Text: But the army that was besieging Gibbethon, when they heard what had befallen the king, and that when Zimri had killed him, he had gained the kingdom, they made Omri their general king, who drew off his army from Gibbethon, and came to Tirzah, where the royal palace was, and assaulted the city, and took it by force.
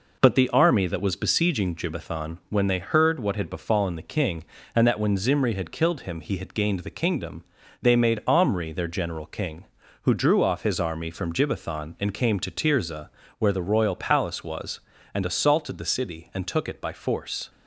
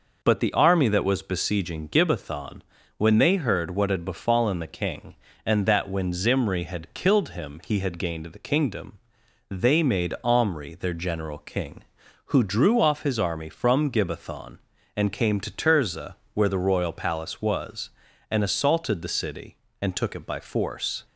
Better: neither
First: none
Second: none

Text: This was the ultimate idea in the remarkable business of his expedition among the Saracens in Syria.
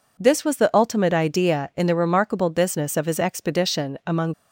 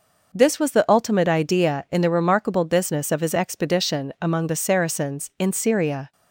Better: second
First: stops before "the Saracens in Syria"; at 4.3 s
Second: none

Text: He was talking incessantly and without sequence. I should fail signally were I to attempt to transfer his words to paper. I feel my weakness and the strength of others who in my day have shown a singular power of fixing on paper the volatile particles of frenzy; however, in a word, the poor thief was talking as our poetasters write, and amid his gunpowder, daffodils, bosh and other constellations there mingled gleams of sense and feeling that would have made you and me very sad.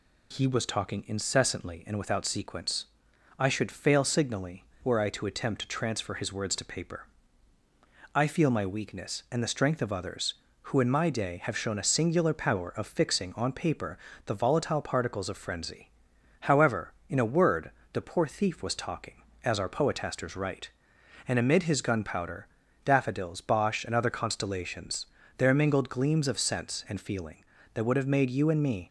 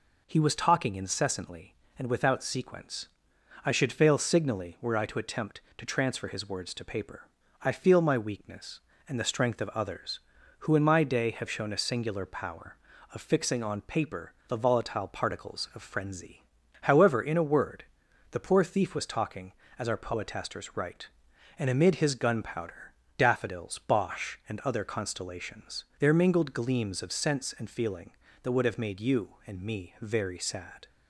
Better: second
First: pauses between "paper" and "the"; slight; at 13.9 s; 0.26 s long // pauses between "constellations" and "there"; slight; at 25.0 s; 0.28 s long // stops before "very sad"; at 28.8 s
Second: pauses between "paper" and "the"; slight; at 14.3 s; 0.16 s long

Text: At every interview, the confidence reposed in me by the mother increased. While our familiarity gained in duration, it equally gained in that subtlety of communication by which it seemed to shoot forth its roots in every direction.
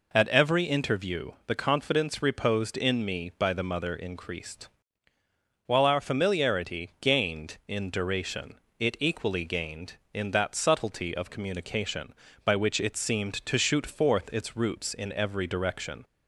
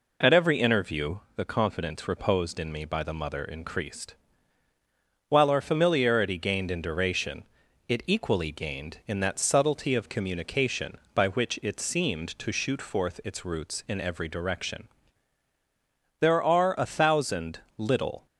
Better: first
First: none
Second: goes on to say "There are a thousand little"; strong; from 16.1 s on; 2.0 s long

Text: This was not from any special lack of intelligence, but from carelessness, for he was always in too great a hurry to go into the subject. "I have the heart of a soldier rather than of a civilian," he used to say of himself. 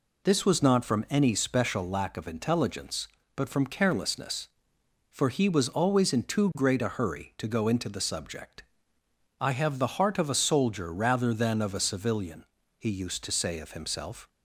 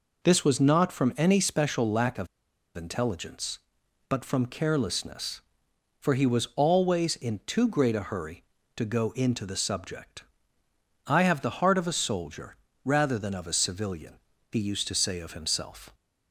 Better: first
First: none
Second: pauses between "of" and "intelligence"; noticeable; at 2.2 s; 0.48 s long // pauses between "soldier" and "rather"; slight; at 12.5 s; 0.28 s long

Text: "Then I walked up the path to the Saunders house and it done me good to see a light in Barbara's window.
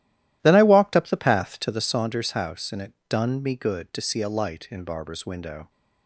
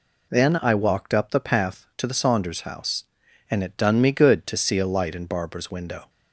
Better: second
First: starts louder than the rest; strong; until 2.0 s; 13.5 dB // pauses between "it" and "done"; slight; at 2.9 s; 0.16 s long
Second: none

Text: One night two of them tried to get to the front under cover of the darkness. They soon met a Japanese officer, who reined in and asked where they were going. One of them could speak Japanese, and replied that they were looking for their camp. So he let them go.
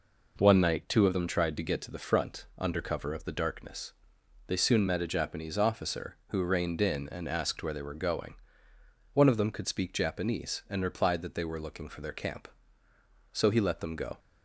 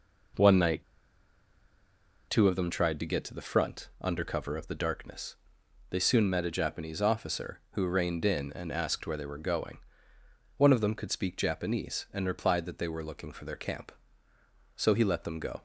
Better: first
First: none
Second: pauses between "night" and "two"; strong; at 0.8 s; 1.4 s long

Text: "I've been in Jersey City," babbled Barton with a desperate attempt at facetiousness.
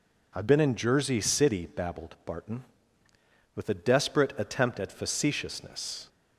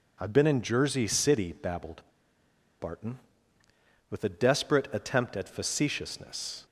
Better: first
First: none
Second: pauses between "babbled" and "Barton"; noticeable; at 2.0 s; 0.76 s long

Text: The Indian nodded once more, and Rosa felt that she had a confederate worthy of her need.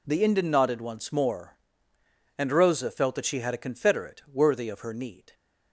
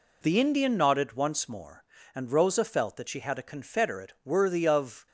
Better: first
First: none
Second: stops before "her need"; at 5.0 s

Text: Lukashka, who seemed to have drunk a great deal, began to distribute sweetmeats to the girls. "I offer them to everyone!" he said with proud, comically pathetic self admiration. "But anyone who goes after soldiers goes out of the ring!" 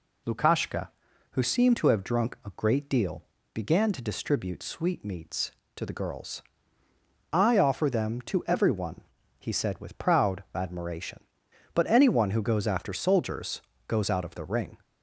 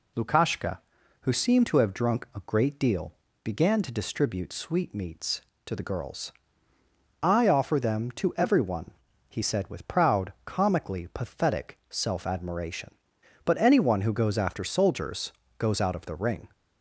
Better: second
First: skips "comically pathetic self"; at 10.4 s // pauses between "soldiers" and "goes"; slight; at 13.5 s; 0.28 s long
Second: pauses between "soldiers" and "goes"; slight; at 15.3 s; 0.28 s long

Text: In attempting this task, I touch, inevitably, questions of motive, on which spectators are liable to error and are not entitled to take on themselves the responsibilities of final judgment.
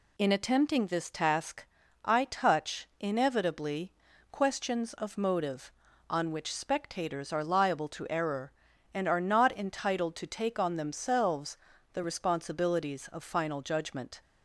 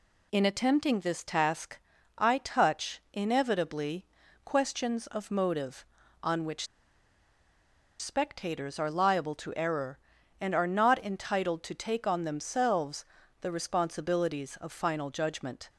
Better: first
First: pauses between "themselves" and "the"; slight; at 11.5 s; 0.34 s long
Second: pauses between "which" and "spectators"; strong; at 6.6 s; 1.3 s long // pauses between "themselves" and "the"; slight; at 13.0 s; 0.34 s long

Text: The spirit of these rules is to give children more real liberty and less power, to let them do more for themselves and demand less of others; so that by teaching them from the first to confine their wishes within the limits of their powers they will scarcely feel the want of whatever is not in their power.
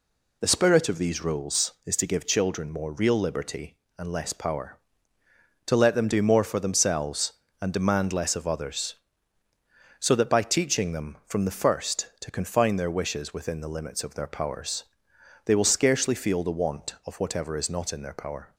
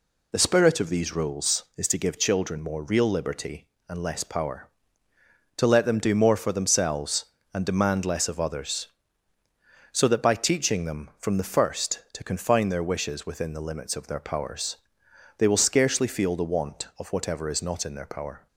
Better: neither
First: pauses between "powers" and "they"; noticeable; at 14.8 s; 0.60 s long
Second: pauses between "powers" and "they"; noticeable; at 14.7 s; 0.60 s long

